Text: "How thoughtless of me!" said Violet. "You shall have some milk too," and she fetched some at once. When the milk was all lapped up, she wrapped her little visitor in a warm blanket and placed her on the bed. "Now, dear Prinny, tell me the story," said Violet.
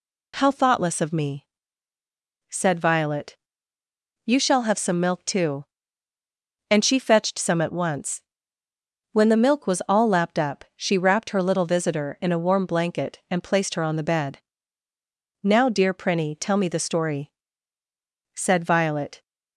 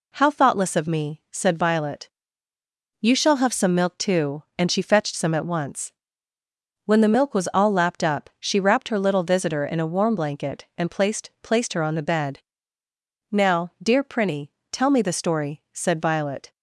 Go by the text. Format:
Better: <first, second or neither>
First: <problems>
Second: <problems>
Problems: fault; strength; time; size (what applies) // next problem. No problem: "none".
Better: first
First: none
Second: says "placed" twice; at 11.4 s